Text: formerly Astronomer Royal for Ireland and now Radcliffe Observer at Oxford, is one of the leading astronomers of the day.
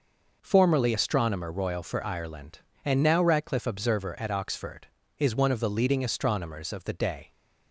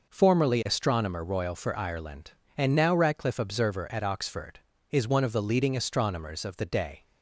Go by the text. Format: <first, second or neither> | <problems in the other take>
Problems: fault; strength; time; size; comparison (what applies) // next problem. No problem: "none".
neither | none